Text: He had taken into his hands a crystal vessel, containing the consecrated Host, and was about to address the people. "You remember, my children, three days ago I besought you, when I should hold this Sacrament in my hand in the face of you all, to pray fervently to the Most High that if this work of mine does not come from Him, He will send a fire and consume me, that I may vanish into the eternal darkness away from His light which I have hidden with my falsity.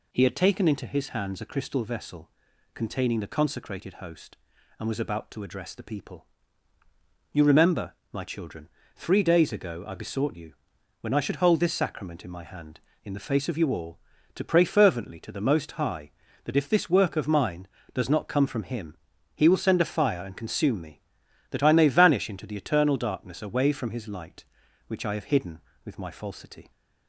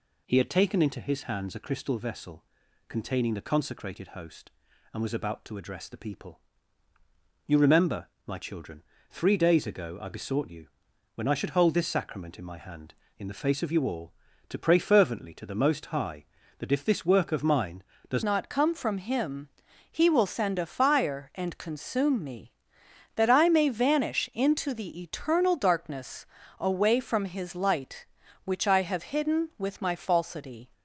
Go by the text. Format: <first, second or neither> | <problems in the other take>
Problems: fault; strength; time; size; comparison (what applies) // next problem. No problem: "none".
first | changes voice at "not"; from 18.2 s on; 12.4 s long // pauses between "darkness" and "away"; slight; at 26.2 s; 0.32 s long